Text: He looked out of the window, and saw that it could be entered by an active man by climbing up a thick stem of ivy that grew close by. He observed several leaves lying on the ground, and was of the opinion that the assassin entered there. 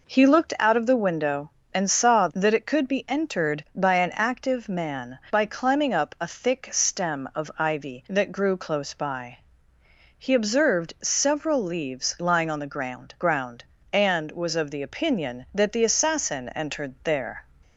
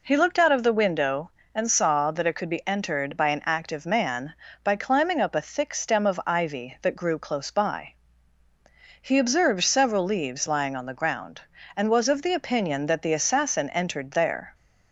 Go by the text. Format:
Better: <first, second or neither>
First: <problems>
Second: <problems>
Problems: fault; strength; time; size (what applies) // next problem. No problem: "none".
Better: second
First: says "ground" twice; at 13.1 s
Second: none